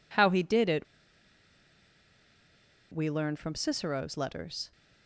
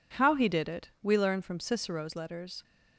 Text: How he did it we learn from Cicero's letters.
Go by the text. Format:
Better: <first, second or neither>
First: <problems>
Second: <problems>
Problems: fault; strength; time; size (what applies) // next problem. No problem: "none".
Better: second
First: pauses between "it" and "we"; strong; at 0.8 s; 2.0 s long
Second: none